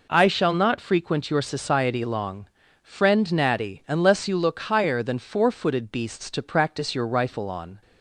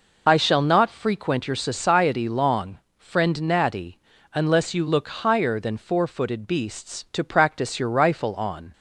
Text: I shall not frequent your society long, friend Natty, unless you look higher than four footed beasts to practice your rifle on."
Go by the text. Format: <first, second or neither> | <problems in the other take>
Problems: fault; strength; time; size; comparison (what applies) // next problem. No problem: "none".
first | loses the start of "I"; at 0.2 s; 30 ms